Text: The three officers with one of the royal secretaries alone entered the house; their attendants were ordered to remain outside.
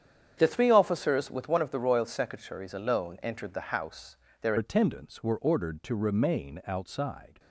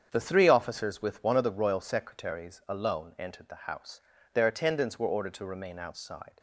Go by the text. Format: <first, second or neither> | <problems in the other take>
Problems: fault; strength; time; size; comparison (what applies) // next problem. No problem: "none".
second | starts louder than the rest; strong; until 1.3 s; 8.5 dB; strong in the second // changes voice at "attendants"; from 4.5 s on; 2.8 s long